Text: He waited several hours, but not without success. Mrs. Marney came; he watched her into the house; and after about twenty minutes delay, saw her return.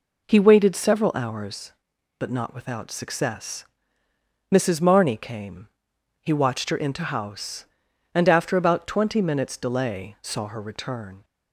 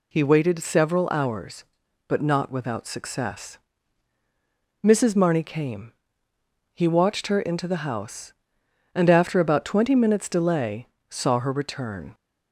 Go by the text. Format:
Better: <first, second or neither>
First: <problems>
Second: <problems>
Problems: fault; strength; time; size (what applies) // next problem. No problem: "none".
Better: second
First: skips "the"; at 7.0 s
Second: none